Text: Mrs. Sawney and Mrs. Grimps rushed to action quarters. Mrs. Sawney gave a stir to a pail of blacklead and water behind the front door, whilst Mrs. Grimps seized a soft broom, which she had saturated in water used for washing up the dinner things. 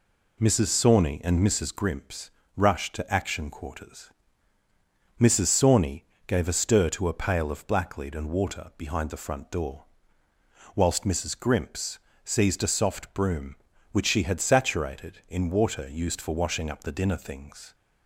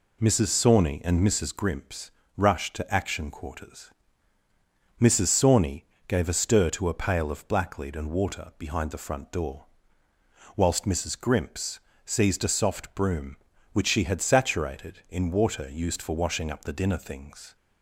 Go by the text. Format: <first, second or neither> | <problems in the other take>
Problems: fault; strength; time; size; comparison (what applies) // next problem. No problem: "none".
neither | pauses between "Grimps" and "rushed"; slight; the same in both // pauses between "Sawney" and "gave"; slight; the same in both // pauses between "Grimps" and "seized"; slight; the same in both